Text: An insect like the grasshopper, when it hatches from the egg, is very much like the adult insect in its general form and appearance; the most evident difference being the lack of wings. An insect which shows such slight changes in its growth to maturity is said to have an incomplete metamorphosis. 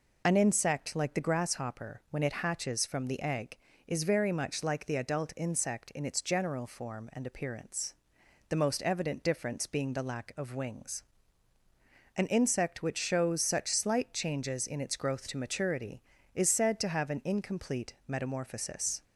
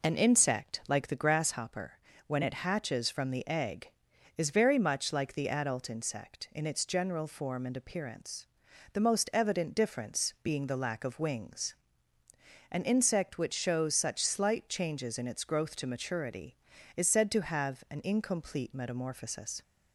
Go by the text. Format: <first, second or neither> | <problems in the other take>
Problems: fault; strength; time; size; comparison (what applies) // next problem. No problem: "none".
neither | none